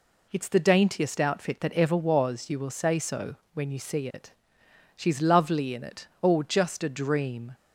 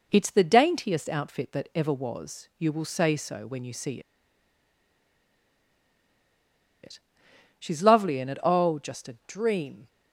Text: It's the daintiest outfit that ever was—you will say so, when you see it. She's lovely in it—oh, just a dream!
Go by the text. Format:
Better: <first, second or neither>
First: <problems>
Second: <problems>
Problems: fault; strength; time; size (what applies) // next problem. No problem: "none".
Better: first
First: none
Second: pauses between "see" and "it"; strong; at 4.0 s; 2.8 s long